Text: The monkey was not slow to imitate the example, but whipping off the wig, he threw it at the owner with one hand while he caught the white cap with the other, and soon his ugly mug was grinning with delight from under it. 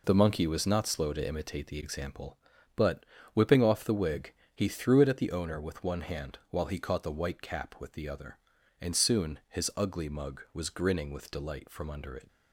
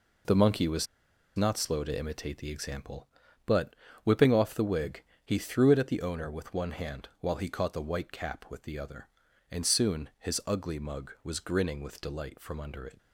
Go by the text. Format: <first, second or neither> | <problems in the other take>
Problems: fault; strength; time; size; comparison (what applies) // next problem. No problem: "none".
first | pauses between "was" and "not"; noticeable; at 0.8 s; 0.51 s long // pauses between "but" and "whipping"; slight; at 3.7 s; 0.30 s long; slight in the first